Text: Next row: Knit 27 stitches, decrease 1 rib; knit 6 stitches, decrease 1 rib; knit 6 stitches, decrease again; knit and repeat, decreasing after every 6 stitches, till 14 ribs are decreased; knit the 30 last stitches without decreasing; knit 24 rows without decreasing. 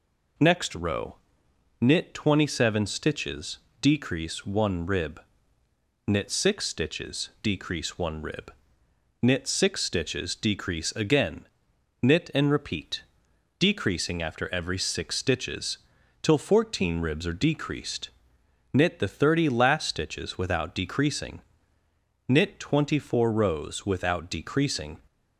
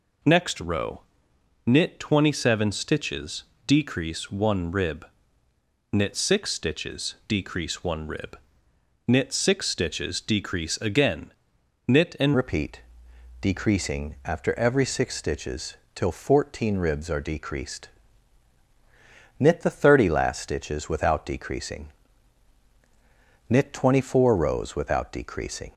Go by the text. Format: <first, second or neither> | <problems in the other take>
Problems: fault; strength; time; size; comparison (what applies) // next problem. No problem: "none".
first | changes voice at "repeat"; from 12.3 s on; 13.4 s long